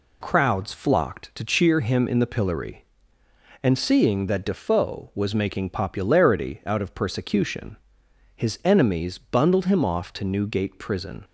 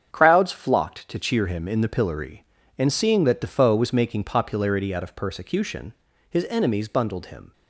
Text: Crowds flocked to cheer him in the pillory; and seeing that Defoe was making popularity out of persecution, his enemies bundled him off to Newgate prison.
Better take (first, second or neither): first